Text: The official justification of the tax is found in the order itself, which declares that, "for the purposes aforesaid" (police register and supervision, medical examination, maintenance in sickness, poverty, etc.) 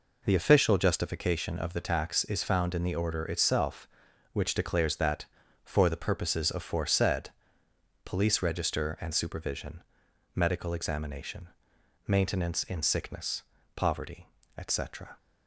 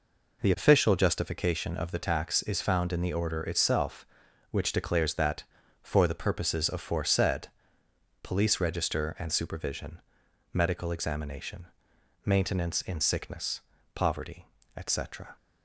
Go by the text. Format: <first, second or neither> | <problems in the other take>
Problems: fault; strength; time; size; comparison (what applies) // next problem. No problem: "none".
neither | none